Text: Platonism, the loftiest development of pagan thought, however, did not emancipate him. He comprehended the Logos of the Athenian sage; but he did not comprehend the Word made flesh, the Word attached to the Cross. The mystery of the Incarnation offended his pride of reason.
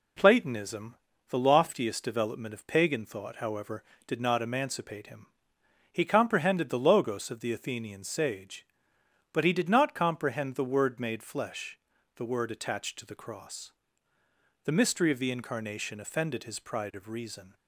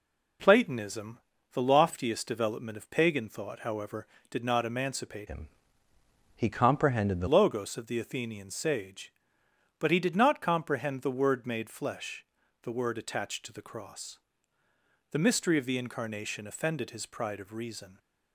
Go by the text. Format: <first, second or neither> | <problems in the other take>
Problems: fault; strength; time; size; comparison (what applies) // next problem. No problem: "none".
first | changes voice from "him" to "the"; from 5.2 to 7.2 s; 2.0 s long